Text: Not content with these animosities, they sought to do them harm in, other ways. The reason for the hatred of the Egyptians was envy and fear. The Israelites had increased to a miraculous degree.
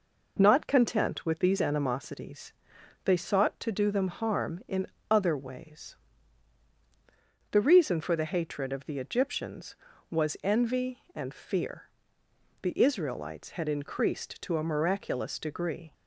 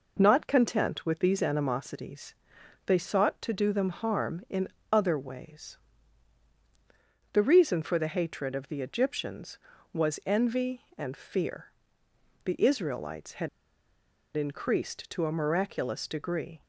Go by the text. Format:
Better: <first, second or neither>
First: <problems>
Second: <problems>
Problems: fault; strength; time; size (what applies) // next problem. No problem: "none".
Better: first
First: none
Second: pauses between "had" and "increased"; noticeable; at 13.4 s; 0.88 s long